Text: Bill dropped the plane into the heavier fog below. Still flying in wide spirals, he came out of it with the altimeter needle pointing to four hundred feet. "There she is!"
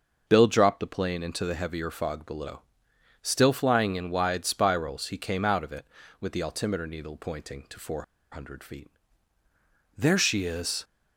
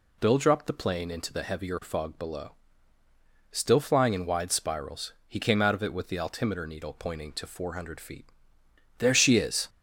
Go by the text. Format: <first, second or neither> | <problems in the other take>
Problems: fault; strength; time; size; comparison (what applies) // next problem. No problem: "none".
second | starts louder than the rest; noticeable; until 1.2 s; 6 dB // pauses between "four" and "hundred"; slight; at 8.0 s; 0.28 s long